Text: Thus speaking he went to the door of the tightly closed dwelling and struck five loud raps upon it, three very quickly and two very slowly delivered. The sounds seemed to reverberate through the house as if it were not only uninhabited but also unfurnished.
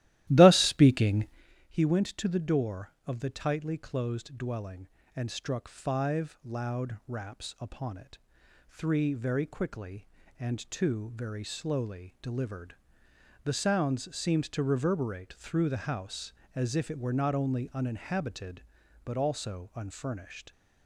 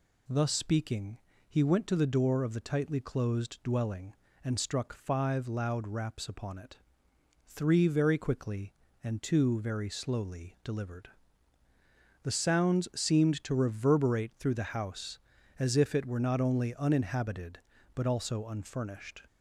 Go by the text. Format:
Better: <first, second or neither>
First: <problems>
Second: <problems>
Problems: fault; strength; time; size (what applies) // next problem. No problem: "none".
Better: second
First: starts louder than the rest; strong; until 1.4 s; 15 dB // pauses between "speaking" and "he"; at 1.2 s; 0.44 s long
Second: pauses between "speaking" and "he"; slight; at 1.1 s; 0.30 s long